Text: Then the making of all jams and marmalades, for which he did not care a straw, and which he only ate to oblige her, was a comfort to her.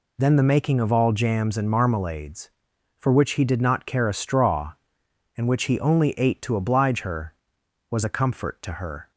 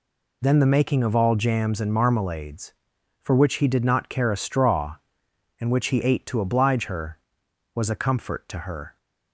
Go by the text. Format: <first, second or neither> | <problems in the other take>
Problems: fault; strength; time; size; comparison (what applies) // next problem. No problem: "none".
first | skips "only"; at 6.0 s